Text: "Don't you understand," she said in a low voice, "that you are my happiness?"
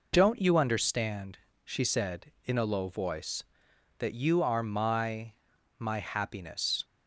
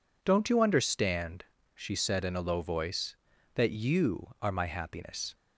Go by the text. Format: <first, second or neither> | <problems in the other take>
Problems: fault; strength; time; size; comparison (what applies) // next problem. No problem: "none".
second | says "my" twice; at 5.7 s